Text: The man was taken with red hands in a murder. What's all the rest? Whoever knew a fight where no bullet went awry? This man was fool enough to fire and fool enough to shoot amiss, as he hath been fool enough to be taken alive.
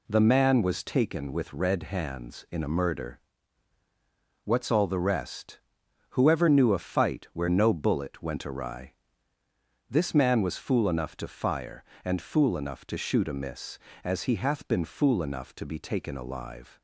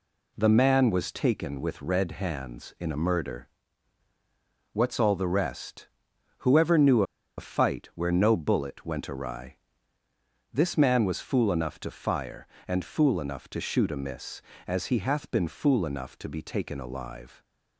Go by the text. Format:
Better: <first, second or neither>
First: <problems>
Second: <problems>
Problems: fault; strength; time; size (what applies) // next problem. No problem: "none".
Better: first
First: none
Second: pauses between "knew" and "a"; slight; at 7.0 s; 0.34 s long